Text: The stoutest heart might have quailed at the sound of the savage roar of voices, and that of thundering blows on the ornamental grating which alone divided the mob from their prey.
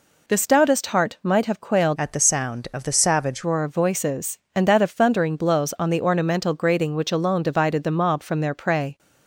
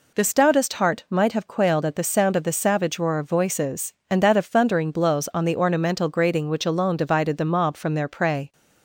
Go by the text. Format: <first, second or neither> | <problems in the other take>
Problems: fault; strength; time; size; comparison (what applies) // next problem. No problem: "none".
second | changes voice from "at" to "savage"; from 1.9 to 3.4 s; 1.5 s long